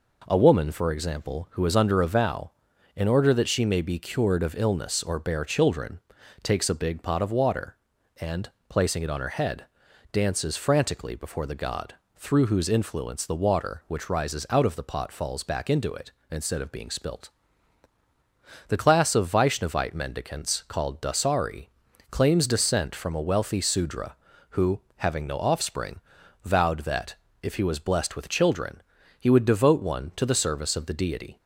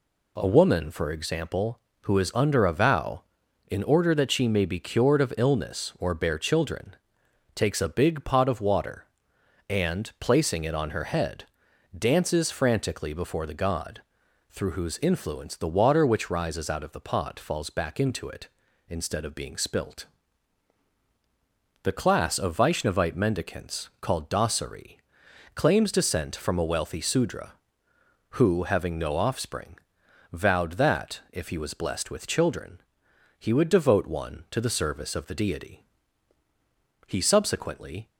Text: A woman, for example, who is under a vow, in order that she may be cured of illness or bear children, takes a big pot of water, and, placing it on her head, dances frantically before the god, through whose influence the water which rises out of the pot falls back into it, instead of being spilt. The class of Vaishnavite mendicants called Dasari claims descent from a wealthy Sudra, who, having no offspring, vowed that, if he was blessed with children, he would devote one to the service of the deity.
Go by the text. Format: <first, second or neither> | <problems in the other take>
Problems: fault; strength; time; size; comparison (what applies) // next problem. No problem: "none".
first | pauses between "Dasari" and "claims"; noticeable; at 24.9 s; 0.56 s long; also in the first // goes on to say "He subsequently"; noticeable; from 37.0 s on; 1.0 s long